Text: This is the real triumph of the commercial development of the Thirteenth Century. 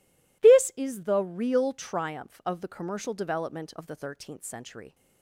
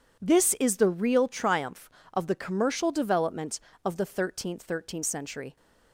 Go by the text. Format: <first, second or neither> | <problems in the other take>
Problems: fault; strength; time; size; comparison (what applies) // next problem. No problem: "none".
first | says "Thirteenth" twice; at 4.6 s